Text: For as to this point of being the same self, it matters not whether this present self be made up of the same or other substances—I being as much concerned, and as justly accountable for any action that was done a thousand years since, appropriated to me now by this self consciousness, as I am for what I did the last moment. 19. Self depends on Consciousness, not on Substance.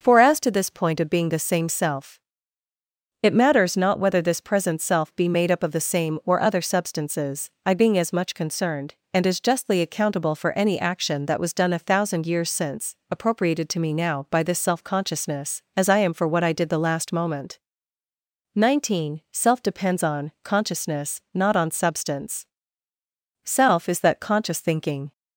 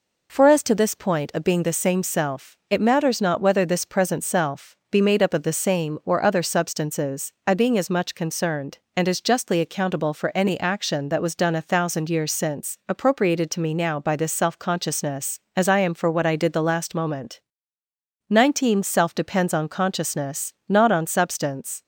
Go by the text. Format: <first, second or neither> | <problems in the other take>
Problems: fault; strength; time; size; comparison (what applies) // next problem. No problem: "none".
second | starts louder than the rest; noticeable; until 1.0 s; 6 dB // goes on to say "SELF is that conscious thinking"; strong; from 23.4 s on; 1.6 s long